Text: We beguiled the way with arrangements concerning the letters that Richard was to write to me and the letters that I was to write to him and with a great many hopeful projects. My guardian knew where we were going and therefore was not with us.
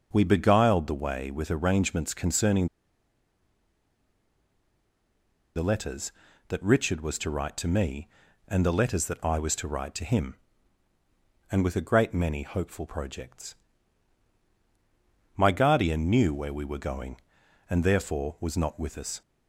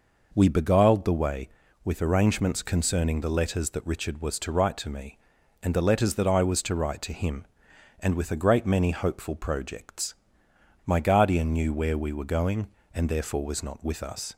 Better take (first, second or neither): second